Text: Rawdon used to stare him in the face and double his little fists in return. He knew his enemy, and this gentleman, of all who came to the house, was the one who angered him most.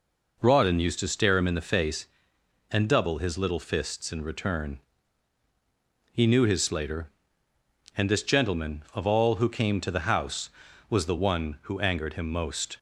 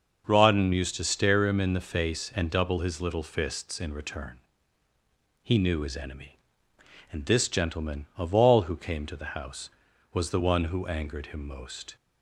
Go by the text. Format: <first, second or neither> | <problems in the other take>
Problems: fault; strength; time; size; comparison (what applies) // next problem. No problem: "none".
second | says "slater" for "enemy"; at 6.6 s